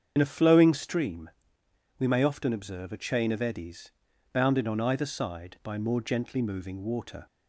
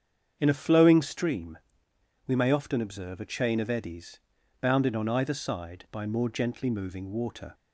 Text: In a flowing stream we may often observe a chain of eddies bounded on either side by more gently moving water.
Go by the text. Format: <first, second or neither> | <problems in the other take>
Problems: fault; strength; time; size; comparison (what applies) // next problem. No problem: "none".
second | loses the start of "In"; at 0.1 s; 45 ms // starts louder than the rest; strong; until 1.1 s; 7.5 dB; strong in the second // pauses between "stream" and "we"; noticeable; at 1.2 s; 0.68 s long; noticeable in the second // pauses between "eddies" and "bounded"; at 3.8 s; 0.42 s long; also in the second